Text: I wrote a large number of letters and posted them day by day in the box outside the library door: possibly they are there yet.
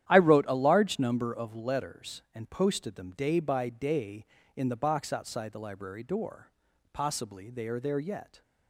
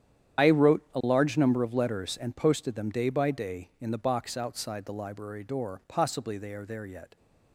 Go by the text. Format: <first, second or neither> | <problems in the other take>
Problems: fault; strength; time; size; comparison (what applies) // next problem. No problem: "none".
first | loses the start of "I"; at 0.3 s; 70 ms // starts louder than the rest; strong; until 1.5 s; 9.5 dB; strong in the first